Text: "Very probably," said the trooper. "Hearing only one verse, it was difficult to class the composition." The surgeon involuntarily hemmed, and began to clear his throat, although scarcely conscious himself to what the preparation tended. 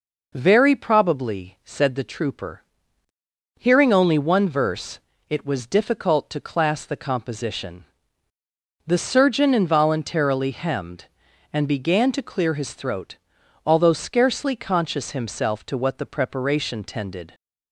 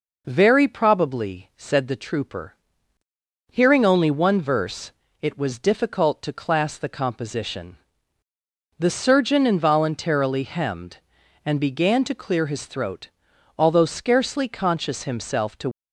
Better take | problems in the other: first | stops before "what the preparation tended"; at 15.7 s

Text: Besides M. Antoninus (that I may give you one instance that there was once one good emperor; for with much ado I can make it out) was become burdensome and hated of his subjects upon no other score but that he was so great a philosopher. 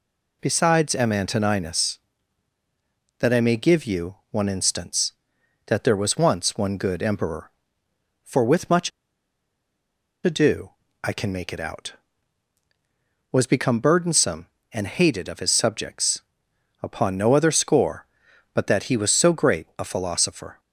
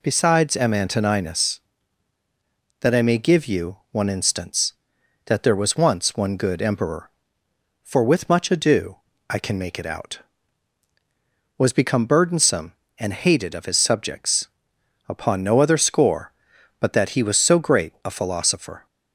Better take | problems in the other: second | pauses between "you" and "one"; slight; at 4.1 s; 0.16 s long; slight in the second // pauses between "much" and "ado"; strong; at 8.9 s; 1.3 s long // pauses between "ado" and "I"; slight; at 10.6 s; 0.32 s long; slight in the second // pauses between "subjects" and "upon"; noticeable; at 16.2 s; 0.62 s long; noticeable in the second

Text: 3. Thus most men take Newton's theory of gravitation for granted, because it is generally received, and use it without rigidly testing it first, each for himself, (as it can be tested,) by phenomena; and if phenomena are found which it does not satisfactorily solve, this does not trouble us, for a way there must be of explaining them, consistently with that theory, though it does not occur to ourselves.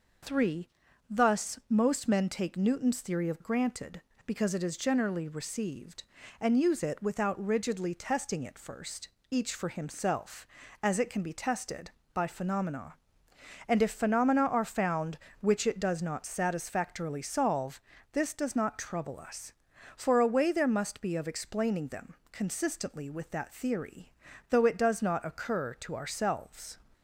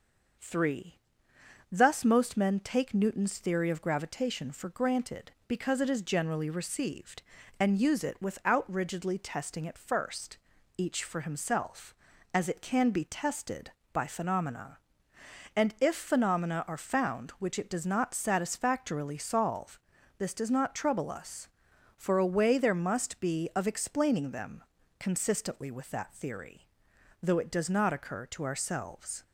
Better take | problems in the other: second | skips "gravitation for"; at 3.4 s

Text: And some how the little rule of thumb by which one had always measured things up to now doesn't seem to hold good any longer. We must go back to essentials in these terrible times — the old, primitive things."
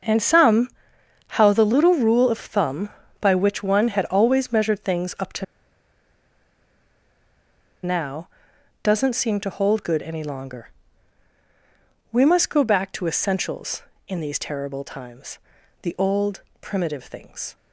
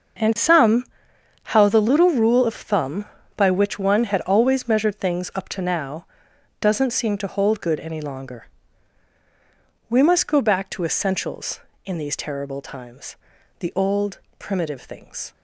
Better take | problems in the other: second | starts louder than the rest; until 1.6 s; 6 dB; also in the second // pauses between "some" and "how"; noticeable; at 0.6 s; 0.60 s long; noticeable in the second // pauses between "to" and "now"; strong; at 5.4 s; 2.3 s long // pauses between "now" and "doesn't"; noticeable; at 8.2 s; 0.54 s long; noticeable in the second

